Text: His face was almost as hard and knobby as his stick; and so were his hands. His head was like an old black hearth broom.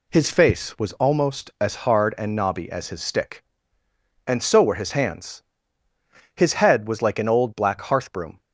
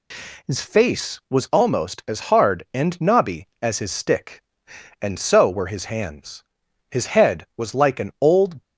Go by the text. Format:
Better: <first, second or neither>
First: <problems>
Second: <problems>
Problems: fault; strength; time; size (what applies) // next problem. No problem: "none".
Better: first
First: none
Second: stops before "black hearth broom"; at 8.6 s